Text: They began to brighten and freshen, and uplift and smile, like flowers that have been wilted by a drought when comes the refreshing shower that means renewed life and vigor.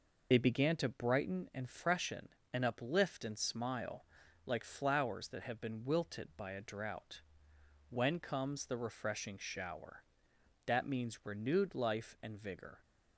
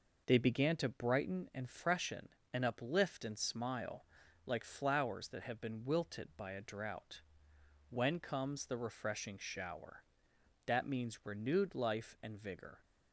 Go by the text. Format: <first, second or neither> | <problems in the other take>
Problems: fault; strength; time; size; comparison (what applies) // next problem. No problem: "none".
second | loses the start of "They"; at 0.3 s; 45 ms // pauses between "drought" and "when"; noticeable; at 7.2 s; 0.66 s long; noticeable in the second